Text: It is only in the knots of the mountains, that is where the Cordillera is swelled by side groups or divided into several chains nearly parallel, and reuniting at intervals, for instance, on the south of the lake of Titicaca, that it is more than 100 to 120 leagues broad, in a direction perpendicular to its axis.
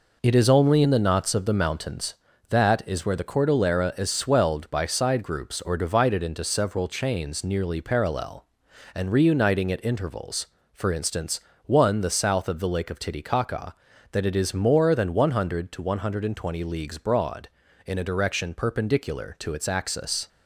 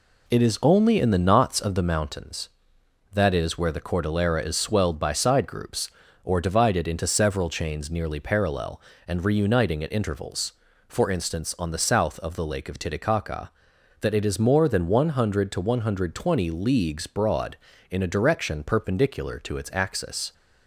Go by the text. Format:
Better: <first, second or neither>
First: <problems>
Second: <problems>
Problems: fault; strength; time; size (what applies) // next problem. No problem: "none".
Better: second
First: says "one" for "on"; at 11.6 s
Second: none